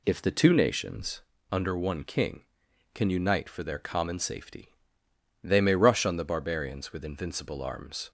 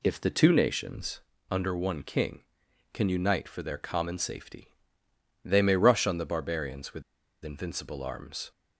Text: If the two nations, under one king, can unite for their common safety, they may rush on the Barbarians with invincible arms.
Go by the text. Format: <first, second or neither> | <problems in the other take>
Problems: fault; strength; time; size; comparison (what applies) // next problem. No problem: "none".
first | pauses between "with" and "invincible"; at 7.0 s; 0.42 s long